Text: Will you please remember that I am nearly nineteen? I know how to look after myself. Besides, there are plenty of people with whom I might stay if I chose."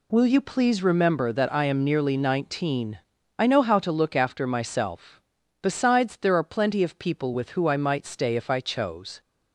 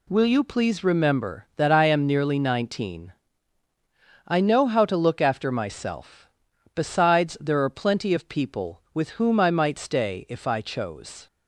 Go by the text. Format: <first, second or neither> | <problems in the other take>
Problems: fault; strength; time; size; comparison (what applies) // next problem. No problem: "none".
second | says "who" for "whom"; at 7.5 s